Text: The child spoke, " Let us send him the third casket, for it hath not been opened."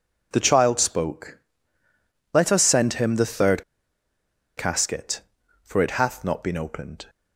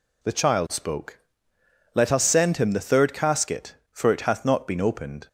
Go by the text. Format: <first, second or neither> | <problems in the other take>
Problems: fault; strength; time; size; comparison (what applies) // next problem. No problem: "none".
second | pauses between "third" and "casket"; noticeable; at 3.6 s; 0.94 s long